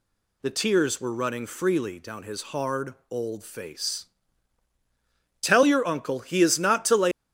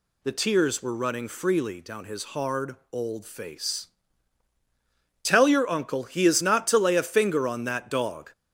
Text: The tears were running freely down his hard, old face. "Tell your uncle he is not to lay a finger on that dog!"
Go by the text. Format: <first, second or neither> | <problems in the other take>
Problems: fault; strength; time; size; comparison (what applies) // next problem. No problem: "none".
second | stops before "a finger on that dog"; at 7.1 s